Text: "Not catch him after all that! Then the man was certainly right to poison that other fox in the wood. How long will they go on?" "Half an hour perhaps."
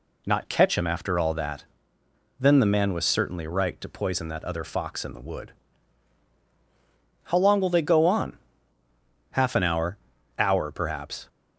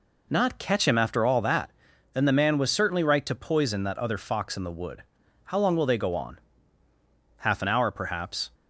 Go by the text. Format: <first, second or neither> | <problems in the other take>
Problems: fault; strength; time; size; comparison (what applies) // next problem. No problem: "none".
second | says "hour" twice; at 10.3 s